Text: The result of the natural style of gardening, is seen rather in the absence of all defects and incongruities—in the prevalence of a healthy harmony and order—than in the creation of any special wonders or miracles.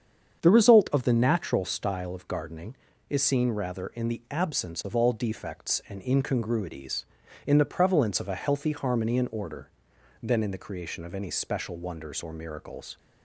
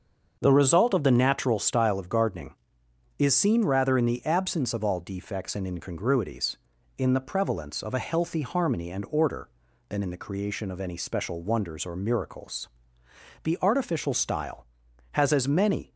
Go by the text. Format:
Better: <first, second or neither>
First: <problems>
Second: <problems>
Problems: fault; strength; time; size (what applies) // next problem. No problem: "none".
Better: first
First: starts louder than the rest; strong; until 1.4 s; 7.5 dB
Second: starts louder than the rest; until 1.4 s; 6.5 dB // goes on to say "The artificial style has as many"; strong; from 13.4 s on; 2.5 s long